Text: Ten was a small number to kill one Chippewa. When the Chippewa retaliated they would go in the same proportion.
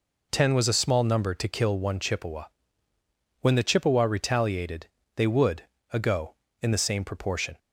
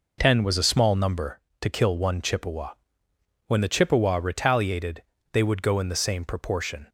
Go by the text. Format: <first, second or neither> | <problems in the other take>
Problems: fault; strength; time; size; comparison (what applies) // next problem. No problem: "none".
second | pauses between "retaliated" and "they"; slight; at 4.8 s; 0.28 s long; slight in the second // says "ago" for "go"; at 5.9 s